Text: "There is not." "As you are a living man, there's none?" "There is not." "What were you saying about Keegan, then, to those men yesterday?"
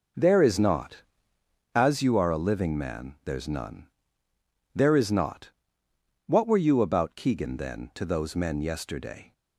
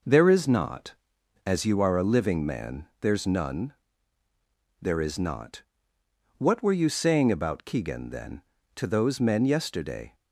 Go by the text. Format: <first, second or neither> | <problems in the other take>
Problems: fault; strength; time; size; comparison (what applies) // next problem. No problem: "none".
second | skips "saying"; at 6.8 s